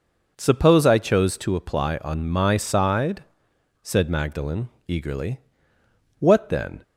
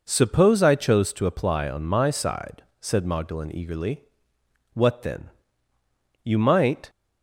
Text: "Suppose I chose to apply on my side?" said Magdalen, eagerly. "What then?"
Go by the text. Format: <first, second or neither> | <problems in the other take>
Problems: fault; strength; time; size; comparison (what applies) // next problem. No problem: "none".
first | goes on to say "You might"; noticeable; from 6.2 s on; 0.66 s long